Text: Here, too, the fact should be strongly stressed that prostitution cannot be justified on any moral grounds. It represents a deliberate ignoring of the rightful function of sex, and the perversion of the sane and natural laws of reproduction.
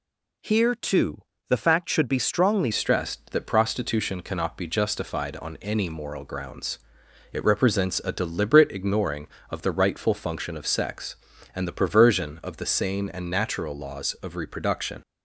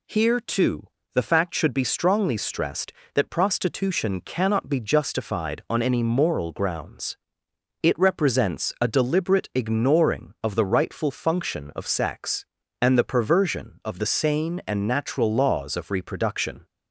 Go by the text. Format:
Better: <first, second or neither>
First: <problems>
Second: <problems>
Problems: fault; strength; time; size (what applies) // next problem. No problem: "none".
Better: second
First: changes voice at "stressed"; from 2.7 s on; 12.3 s long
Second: none